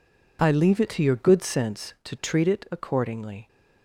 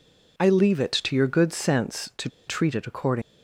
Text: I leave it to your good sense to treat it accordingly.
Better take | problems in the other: first | pauses between "to" and "treat"; slight; at 2.2 s; 0.19 s long

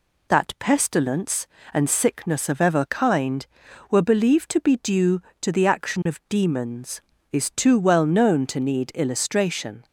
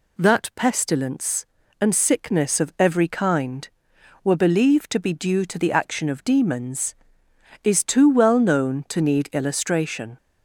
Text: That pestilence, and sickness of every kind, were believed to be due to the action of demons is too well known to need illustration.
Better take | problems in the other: second | says "ever" for "every"; at 2.6 s

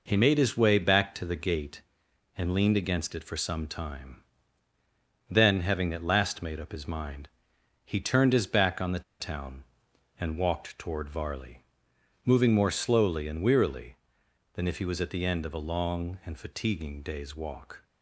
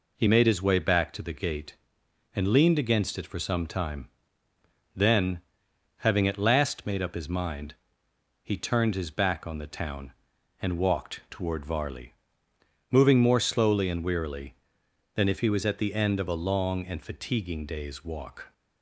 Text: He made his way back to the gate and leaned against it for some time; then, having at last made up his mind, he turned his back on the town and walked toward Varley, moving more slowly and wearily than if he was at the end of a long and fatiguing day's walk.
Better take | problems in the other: second | pauses between "the" and "town"; slight; at 9.0 s; 0.19 s long

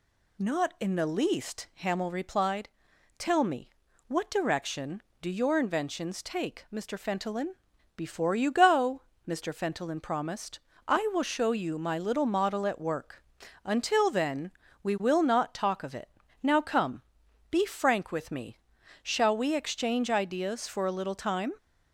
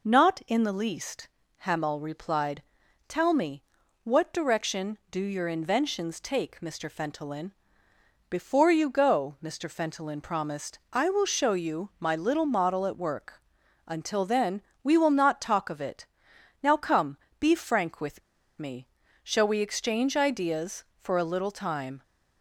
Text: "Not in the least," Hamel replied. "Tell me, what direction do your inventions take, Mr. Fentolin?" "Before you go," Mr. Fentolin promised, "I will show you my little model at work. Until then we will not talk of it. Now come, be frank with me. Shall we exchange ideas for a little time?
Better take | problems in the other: first | pauses between "then" and "we"; slight; at 14.6 s; 0.24 s long; slight in the first // pauses between "with" and "me"; at 18.2 s; 0.38 s long

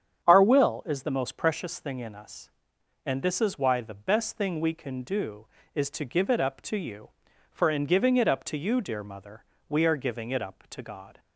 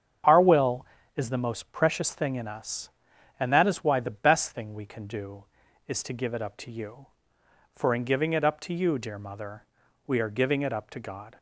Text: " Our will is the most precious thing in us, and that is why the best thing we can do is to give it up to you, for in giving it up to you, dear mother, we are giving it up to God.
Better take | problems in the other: second | starts louder than the rest; strong; until 1.2 s; 8.5 dB; strong in the second // says "this" for "that"; at 3.2 s

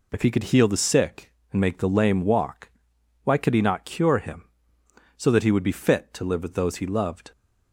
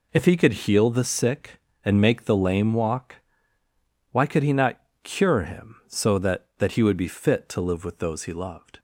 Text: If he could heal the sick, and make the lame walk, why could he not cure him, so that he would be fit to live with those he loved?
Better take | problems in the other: first | pauses between "not" and "cure"; slight; at 4.7 s; 0.24 s long // says "that" twice; at 6.5 s

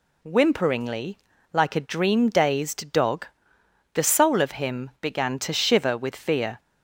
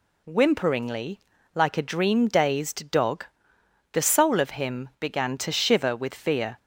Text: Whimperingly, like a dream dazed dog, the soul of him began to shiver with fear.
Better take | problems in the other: neither | none

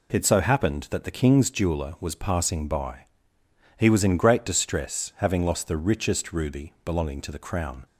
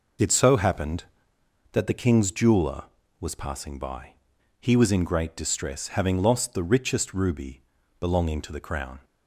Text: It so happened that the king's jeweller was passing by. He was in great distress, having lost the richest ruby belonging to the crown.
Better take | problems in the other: first | loses the start of "It"; at 0.1 s; 45 ms // pauses between "ruby" and "belonging"; at 7.6 s; 0.38 s long

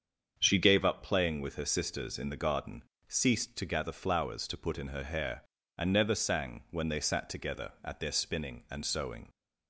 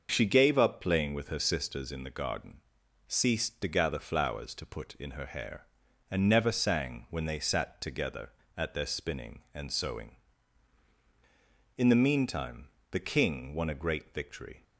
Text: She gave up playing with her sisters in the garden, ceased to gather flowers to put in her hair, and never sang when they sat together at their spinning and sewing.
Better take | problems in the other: first | starts louder than the rest; until 1.1 s; 6.5 dB; strong in the first // goes on to say "In the meantime the King won a great victory"; strong; from 11.7 s on; 2.8 s long

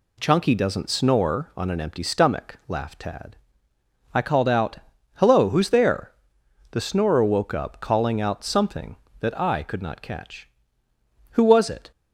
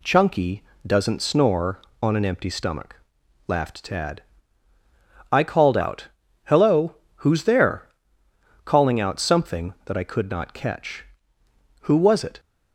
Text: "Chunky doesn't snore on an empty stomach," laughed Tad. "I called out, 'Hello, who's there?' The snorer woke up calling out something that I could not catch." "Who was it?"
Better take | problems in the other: first | pauses between "Chunky" and "doesn't"; slight; at 0.6 s; 0.20 s long // skips "The snorer woke up"; at 8.2 s

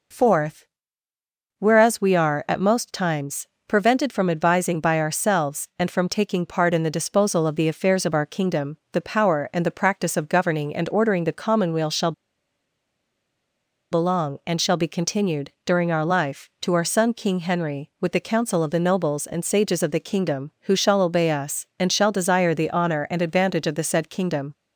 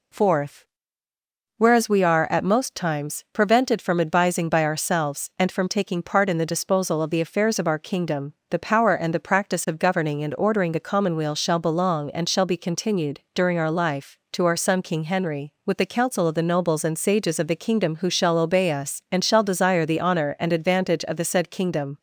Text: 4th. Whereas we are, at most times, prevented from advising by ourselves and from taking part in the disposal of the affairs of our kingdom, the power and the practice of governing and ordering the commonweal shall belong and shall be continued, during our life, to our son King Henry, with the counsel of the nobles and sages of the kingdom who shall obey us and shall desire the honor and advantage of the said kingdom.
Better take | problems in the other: second | pauses between "shall" and "belong"; strong; at 12.1 s; 1.8 s long

